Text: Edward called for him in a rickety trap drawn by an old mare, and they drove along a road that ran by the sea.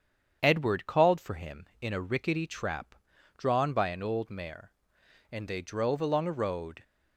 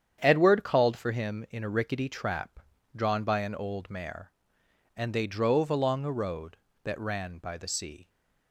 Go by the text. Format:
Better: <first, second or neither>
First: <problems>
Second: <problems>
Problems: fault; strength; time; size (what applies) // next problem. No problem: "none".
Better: second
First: starts louder than the rest; strong; until 1.4 s; 8 dB // pauses between "trap" and "drawn"; at 2.9 s; 0.42 s long // stops before "that ran by the sea"; at 6.8 s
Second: starts louder than the rest; strong; until 1.2 s; 8.5 dB // pauses between "trap" and "drawn"; slight; at 2.5 s; 0.34 s long